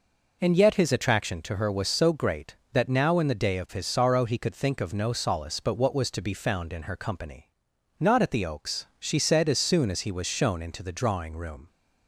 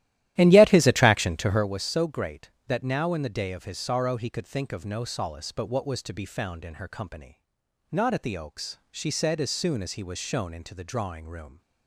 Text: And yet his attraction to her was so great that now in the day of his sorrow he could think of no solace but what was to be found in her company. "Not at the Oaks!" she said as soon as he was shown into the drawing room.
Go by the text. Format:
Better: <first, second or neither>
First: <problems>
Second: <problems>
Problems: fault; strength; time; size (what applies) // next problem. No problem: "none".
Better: first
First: none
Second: starts louder than the rest; strong; until 1.7 s; 14 dB